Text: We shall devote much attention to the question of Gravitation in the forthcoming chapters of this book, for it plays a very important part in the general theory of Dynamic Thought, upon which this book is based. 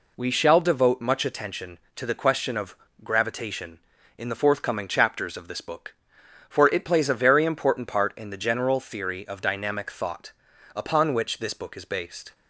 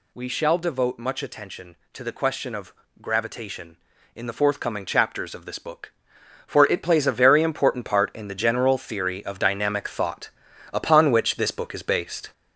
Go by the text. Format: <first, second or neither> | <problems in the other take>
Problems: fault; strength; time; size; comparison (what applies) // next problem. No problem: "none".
first | gets louder; noticeable; throughout; 5 dB // pauses between "of" and "Gravitation"; slight; at 2.7 s; 0.28 s long; slight in the first